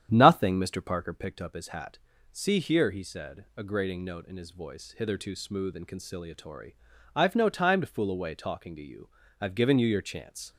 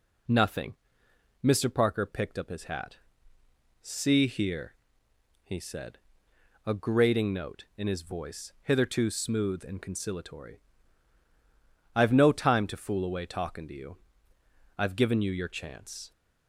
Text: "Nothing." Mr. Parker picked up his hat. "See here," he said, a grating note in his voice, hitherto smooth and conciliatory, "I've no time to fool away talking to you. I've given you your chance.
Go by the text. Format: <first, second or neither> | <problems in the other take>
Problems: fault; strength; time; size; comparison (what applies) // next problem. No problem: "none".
second | starts louder than the rest; strong; until 1.3 s; 9.5 dB